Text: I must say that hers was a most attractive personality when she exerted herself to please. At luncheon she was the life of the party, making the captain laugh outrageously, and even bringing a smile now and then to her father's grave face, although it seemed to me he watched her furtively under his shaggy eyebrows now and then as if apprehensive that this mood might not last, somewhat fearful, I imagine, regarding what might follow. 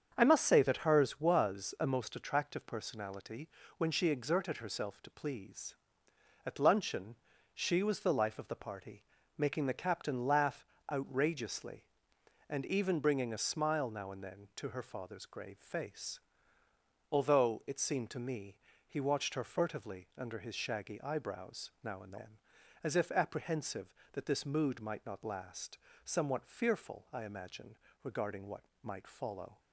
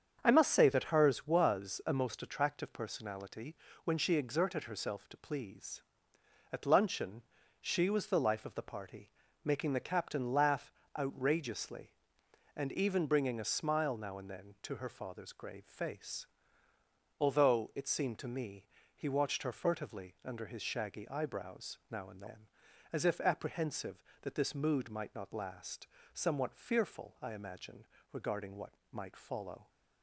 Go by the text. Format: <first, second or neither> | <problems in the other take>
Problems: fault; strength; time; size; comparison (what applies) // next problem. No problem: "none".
neither | starts louder than the rest; strong; the same in both // pauses between "personality" and "when"; slight; the same in both // pauses between "luncheon" and "she"; the same in both // pauses between "laugh" and "outrageously"; slight; the same in both // pauses between "me" and "he"; slight; the same in both // pauses between "what" and "might"; slight; the same in both